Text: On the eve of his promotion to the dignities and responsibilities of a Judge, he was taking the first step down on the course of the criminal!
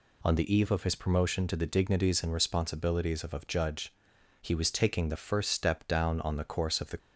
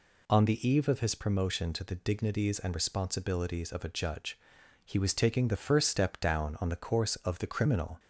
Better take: second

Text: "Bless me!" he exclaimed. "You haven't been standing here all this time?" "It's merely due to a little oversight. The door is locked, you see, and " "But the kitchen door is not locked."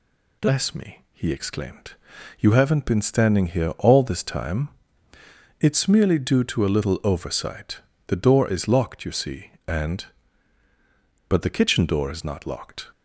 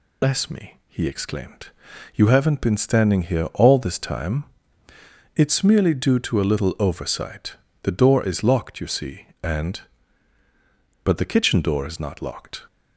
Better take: first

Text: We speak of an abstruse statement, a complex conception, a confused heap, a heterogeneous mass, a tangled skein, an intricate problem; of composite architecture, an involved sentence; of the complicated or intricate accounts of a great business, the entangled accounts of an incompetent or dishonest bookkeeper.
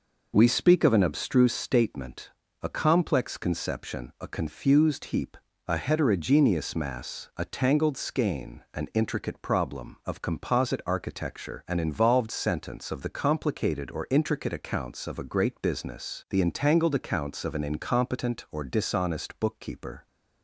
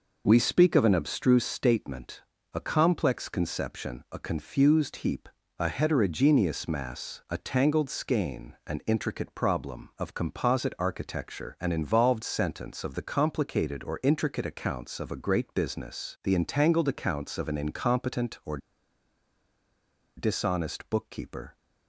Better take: first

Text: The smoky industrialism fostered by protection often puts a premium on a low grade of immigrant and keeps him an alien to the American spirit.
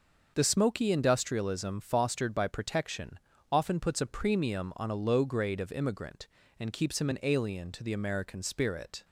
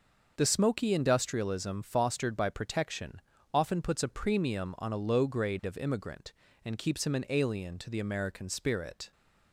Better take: neither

